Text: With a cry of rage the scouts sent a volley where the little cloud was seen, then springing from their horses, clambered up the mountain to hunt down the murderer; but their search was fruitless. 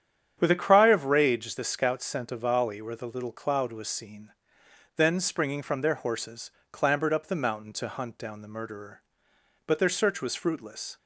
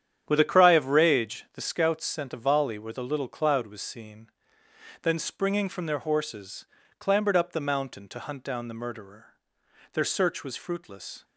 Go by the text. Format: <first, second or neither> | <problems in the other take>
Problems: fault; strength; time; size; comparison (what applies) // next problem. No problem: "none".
first | starts louder than the rest; strong; until 1.2 s; 9 dB; strong in the first // skips "but"; at 9.6 s